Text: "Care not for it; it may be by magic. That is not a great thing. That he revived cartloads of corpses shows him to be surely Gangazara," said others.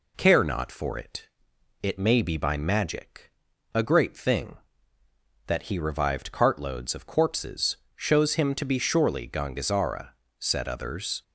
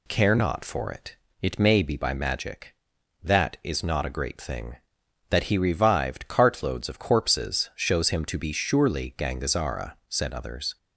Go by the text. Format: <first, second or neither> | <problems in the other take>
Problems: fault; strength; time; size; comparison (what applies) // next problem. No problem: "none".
second | skips "That is not"; at 3.5 s // pauses between "corpses" and "shows"; slight; at 7.7 s; 0.22 s long